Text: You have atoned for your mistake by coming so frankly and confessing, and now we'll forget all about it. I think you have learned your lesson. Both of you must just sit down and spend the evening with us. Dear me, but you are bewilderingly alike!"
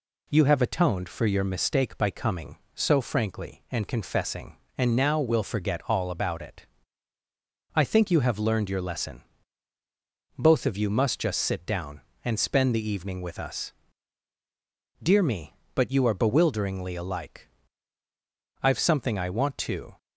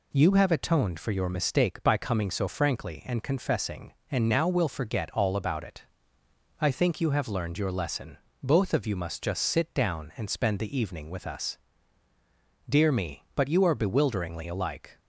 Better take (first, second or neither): second